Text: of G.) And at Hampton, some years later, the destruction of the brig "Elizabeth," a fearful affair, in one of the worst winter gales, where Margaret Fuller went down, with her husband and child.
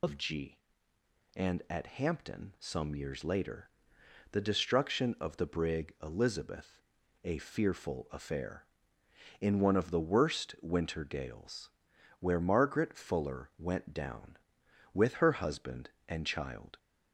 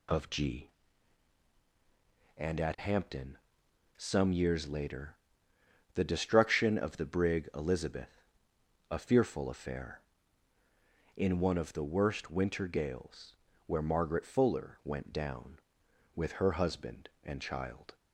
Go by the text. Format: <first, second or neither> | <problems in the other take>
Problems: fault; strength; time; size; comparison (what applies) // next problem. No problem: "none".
second | loses the start of "of"; at 0.0 s; 70 ms